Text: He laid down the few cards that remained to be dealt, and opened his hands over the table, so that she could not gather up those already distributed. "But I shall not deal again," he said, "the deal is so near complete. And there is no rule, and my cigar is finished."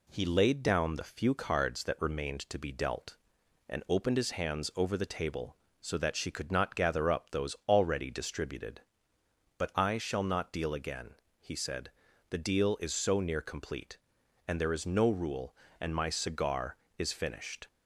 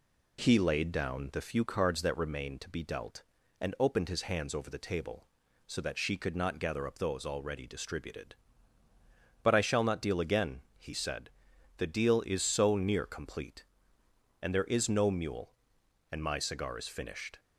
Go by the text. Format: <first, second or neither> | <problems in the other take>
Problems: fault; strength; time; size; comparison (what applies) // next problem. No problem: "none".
first | says "mule" for "rule"; at 15.1 s